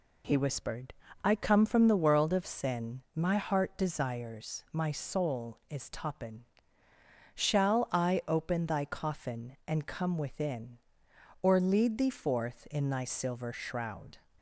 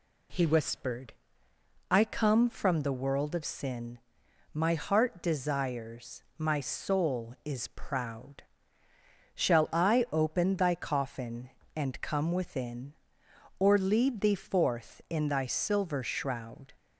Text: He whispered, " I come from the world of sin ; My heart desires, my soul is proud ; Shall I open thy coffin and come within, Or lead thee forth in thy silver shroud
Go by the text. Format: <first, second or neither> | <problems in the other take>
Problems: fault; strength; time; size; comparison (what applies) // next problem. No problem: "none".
second | says "toppin" for "proud"; at 5.8 s